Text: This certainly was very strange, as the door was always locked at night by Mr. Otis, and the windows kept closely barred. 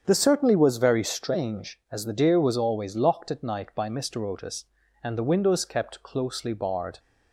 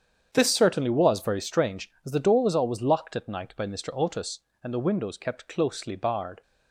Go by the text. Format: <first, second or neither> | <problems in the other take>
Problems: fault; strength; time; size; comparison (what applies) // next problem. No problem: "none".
second | starts louder than the rest; strong; until 1.0 s; 8 dB; strong in the second // says "deer" for "door"; at 2.1 s